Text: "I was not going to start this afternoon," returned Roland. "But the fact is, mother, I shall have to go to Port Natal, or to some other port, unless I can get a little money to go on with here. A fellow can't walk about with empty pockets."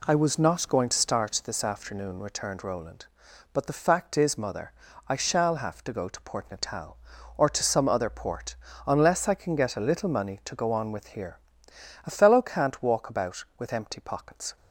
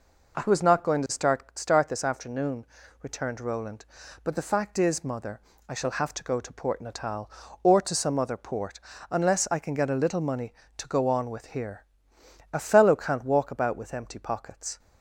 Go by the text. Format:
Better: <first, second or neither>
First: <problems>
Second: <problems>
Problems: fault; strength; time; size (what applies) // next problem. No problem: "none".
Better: first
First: none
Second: says "start" twice; at 1.5 s